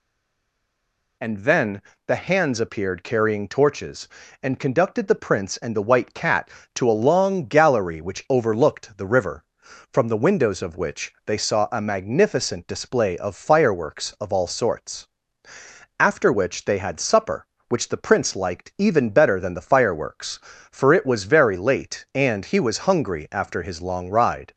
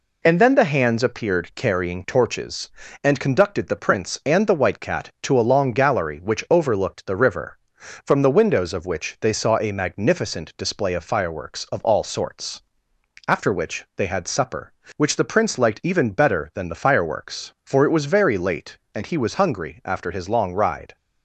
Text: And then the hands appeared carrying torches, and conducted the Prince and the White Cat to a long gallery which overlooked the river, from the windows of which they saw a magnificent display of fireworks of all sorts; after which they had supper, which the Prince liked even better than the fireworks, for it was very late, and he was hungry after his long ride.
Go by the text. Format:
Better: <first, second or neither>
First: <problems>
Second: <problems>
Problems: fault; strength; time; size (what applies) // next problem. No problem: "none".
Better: second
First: stays silent before the first word; noticeable; until 1.2 s; 1.2 s long // pauses between "then" and "the"; slight; at 1.8 s; 0.28 s long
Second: none